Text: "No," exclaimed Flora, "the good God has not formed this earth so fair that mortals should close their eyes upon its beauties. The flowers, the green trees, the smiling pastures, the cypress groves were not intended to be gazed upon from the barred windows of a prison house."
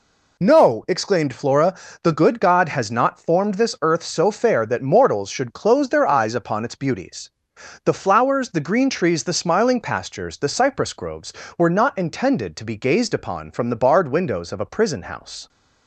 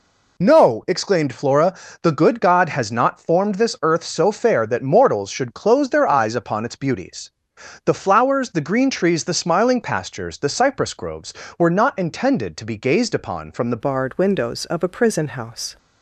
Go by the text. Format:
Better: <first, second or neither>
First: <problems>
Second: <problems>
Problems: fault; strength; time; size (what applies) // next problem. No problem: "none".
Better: first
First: none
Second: changes voice at "barred"; from 13.8 s on; 1.9 s long